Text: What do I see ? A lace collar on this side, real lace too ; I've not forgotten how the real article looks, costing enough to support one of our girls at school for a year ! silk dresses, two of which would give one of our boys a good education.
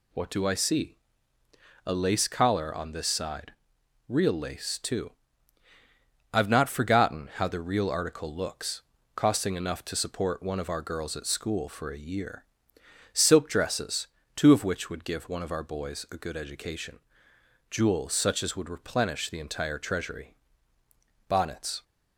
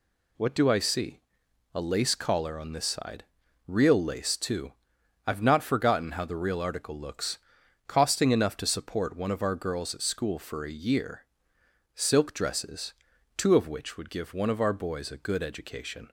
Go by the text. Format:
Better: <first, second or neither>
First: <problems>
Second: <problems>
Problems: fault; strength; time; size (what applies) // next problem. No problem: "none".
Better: second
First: goes on to say "Jewels such as would replenish the entire treasury Bonnets"; strong; from 17.6 s on; 4.1 s long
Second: none